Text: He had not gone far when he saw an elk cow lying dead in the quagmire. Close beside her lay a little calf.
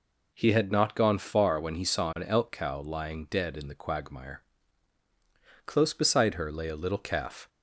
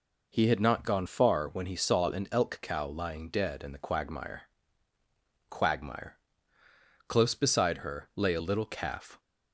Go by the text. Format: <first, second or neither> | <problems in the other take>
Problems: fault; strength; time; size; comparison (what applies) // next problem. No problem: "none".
first | says "quagmire" twice; at 5.4 s